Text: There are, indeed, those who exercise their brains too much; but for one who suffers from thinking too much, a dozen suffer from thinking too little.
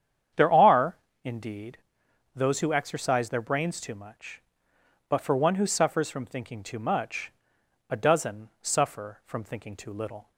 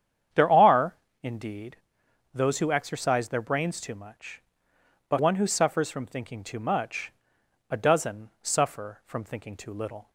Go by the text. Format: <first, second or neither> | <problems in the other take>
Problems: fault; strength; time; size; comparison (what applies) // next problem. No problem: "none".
first | starts louder than the rest; strong; until 1.6 s; 8.5 dB; strong in the first // skips "for"; at 5.1 s